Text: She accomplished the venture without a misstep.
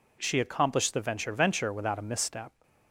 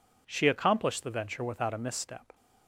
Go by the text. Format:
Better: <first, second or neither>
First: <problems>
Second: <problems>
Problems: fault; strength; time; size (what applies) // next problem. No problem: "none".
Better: second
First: says "venture" twice; at 1.3 s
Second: none